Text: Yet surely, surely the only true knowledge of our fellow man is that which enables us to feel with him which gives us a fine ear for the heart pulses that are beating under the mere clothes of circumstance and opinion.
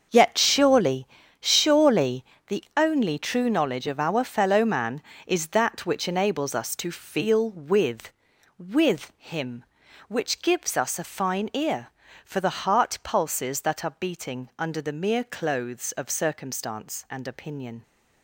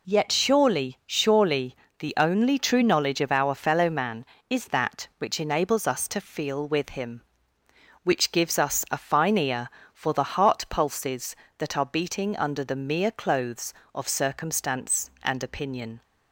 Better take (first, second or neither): second